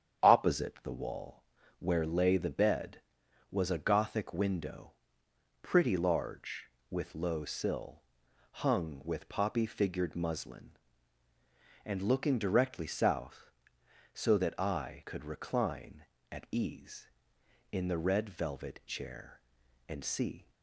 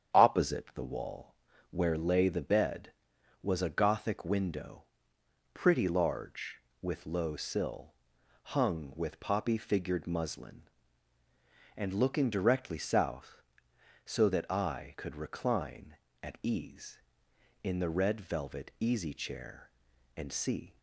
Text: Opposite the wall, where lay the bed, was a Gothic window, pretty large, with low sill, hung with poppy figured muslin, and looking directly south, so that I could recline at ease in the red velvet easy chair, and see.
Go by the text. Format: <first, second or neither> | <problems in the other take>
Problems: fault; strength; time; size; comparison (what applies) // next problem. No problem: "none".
second | starts louder than the rest; strong; until 1.3 s; 8.5 dB; strong in the second // skips "easy"; at 18.8 s